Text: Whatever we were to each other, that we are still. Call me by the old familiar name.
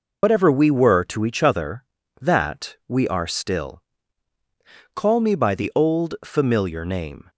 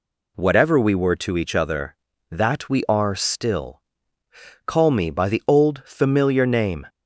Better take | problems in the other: second | loses the start of "Whatever"; at 0.2 s; 95 ms

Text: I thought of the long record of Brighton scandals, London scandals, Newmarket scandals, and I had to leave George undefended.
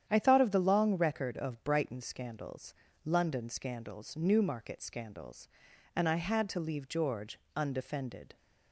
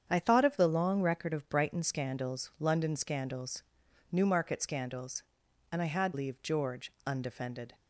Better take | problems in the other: first | starts louder than the rest; strong; until 1.1 s; 8 dB; strong in the first // skips "to"; at 6.1 s // pauses between "George" and "undefended"; slight; at 6.9 s; 0.16 s long; slight in the first

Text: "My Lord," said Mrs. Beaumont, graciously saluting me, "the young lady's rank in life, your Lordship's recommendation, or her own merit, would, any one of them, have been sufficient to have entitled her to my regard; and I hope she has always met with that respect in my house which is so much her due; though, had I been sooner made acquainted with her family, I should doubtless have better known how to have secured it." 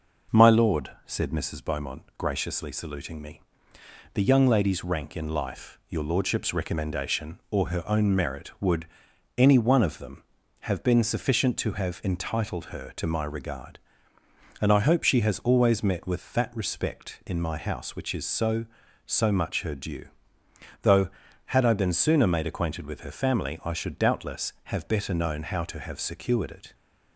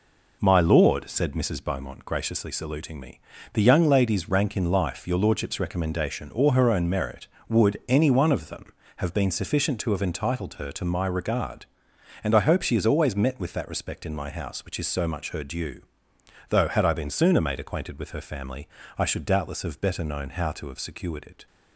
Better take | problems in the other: second | says "so" twice; at 19.0 s

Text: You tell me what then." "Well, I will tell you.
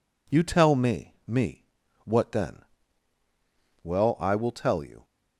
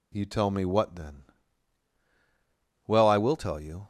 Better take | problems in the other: second | says "me" twice; at 1.2 s

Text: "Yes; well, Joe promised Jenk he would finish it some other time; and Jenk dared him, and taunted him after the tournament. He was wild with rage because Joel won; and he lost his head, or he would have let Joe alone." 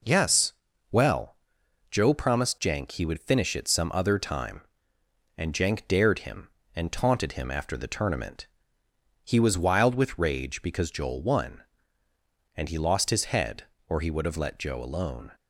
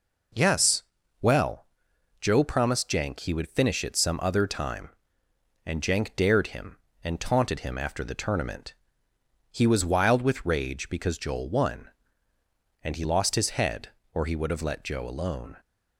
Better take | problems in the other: neither | none

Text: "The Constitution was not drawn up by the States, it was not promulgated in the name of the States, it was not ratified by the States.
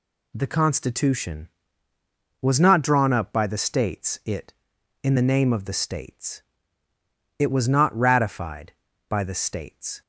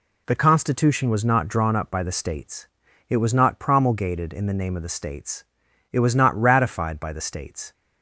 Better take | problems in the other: second | skips "was not promulgated"; at 4.7 s

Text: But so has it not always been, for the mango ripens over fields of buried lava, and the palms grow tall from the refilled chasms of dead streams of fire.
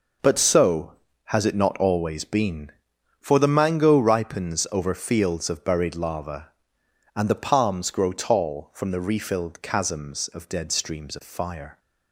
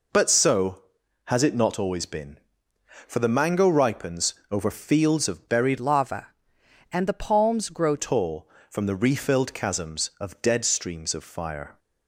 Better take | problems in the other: first | pauses between "ripens" and "over"; slight; at 4.3 s; 0.16 s long // changes voice from "lava" to "grow"; from 5.7 to 7.9 s; 2.2 s long

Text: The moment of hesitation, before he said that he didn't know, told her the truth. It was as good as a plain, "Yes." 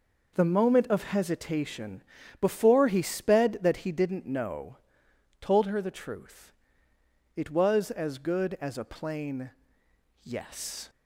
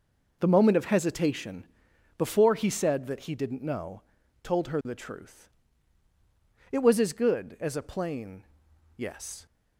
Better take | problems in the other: second | says "sped" for "said"; at 3.0 s

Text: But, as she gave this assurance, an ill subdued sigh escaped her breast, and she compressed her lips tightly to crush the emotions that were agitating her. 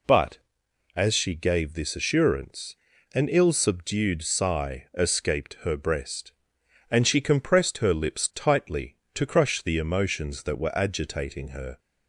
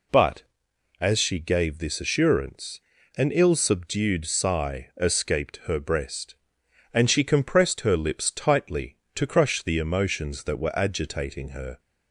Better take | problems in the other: neither | none

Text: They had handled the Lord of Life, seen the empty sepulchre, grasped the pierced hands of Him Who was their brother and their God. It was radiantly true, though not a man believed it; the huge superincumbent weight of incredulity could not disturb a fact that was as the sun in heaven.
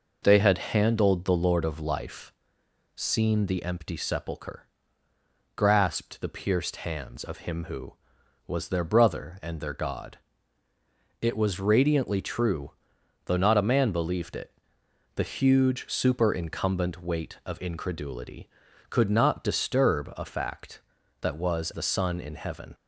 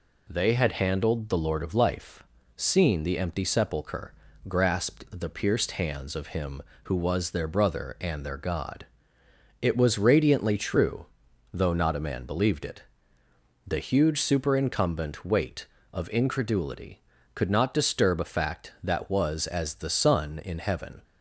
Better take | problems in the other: second | skips "as"; at 21.7 s

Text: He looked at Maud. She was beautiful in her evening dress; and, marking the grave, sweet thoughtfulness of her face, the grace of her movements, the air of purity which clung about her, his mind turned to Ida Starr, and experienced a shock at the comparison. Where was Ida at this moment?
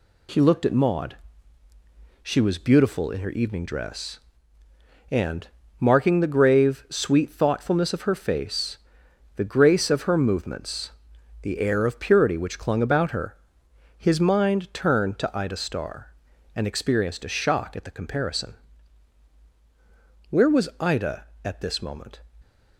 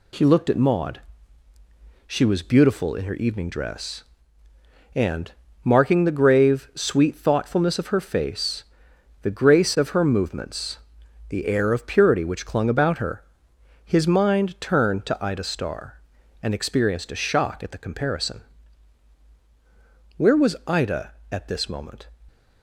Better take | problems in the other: neither | none

